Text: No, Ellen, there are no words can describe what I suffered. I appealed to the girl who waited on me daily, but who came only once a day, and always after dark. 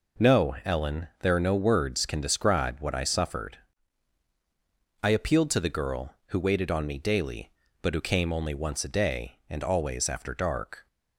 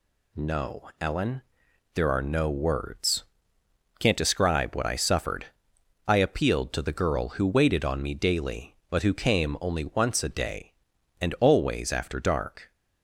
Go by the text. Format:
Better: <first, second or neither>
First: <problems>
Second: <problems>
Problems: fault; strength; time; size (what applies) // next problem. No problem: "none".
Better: first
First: none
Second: says "can't" for "can"; at 3.9 s